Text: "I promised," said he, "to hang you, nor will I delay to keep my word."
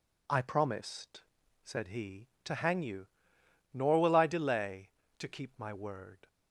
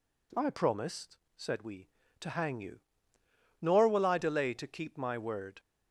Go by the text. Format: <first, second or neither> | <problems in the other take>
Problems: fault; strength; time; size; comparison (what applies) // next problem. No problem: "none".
first | says "we" for "he"; at 1.6 s